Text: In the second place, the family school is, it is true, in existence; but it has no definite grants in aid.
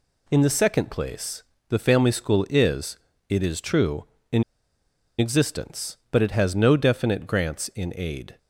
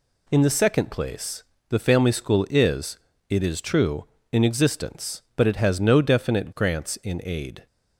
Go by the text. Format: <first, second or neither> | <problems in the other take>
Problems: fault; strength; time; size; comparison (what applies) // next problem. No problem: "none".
second | pauses between "in" and "existence"; noticeable; at 4.4 s; 0.76 s long